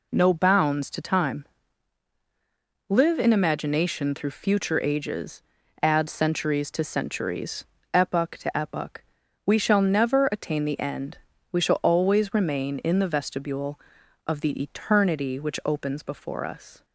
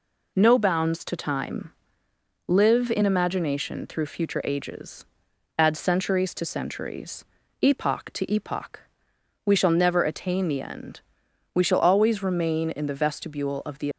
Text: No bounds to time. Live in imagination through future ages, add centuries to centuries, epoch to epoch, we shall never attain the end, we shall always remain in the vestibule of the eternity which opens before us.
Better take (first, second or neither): first